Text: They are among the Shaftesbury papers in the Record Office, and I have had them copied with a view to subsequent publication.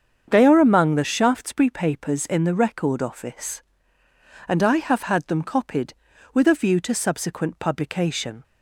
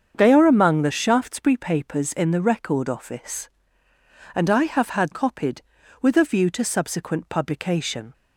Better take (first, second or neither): first